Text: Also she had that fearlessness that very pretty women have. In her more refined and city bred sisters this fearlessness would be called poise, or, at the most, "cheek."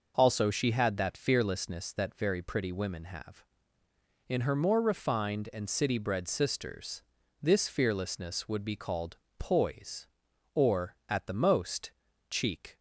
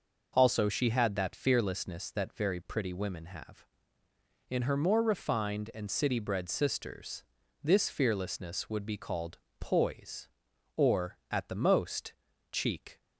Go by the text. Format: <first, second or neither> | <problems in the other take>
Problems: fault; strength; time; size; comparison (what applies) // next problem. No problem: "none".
neither | pauses between "sisters" and "this"; the same in both // pauses between "called" and "poise"; slight; the same in both